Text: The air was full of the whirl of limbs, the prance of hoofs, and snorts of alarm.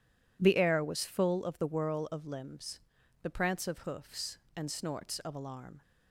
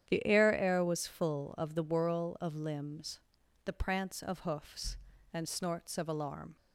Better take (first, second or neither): first